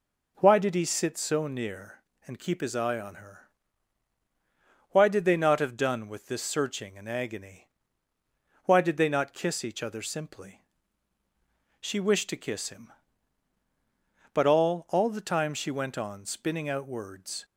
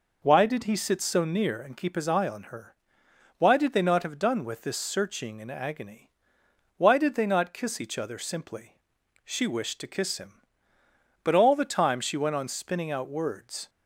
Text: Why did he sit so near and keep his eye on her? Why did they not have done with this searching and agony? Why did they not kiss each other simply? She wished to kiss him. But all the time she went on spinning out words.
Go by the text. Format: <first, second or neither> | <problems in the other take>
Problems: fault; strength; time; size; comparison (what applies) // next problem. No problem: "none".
second | says "all" twice; at 14.8 s